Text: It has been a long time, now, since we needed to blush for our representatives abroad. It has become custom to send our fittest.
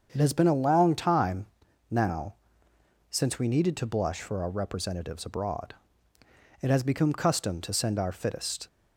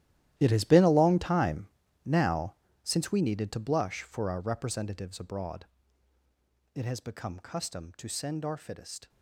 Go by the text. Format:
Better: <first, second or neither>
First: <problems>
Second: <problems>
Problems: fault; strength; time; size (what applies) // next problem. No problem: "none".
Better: first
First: starts louder than the rest; until 1.1 s; 7 dB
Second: gets quieter; strong; throughout; 15.5 dB // starts louder than the rest; strong; until 1.3 s; 13 dB